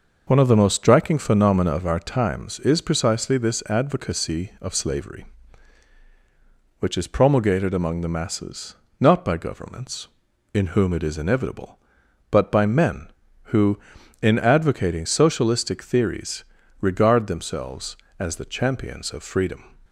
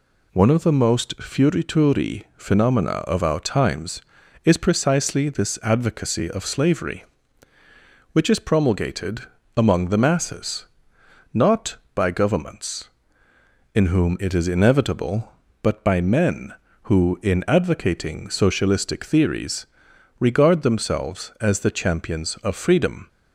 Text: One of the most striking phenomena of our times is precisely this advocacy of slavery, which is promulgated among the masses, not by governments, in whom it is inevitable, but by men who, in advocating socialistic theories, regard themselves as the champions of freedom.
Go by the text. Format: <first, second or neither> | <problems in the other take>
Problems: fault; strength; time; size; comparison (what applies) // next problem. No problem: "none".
first | says "fiorituri" for "striking"; at 1.1 s // pauses between "promulgated" and "among"; slight; at 9.2 s; 0.34 s long